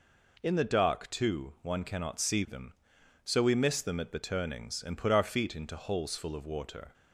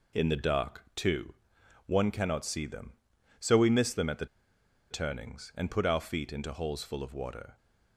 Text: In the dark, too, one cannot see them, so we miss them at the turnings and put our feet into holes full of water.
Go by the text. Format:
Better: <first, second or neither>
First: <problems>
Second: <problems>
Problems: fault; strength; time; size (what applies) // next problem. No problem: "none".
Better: first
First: none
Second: pauses between "the" and "turnings"; noticeable; at 4.2 s; 0.64 s long